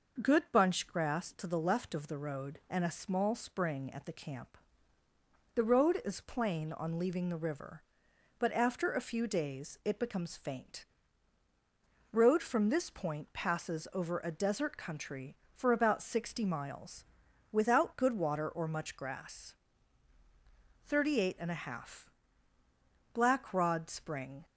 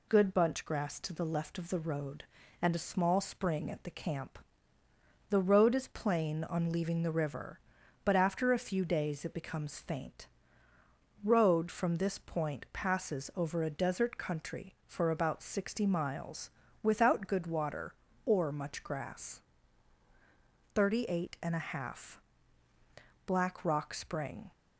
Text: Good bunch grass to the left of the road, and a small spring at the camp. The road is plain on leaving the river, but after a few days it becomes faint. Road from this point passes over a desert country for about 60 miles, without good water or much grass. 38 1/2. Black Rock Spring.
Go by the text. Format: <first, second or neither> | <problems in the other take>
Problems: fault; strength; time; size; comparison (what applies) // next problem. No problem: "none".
second | says "Rod" for "Rock"; at 23.5 s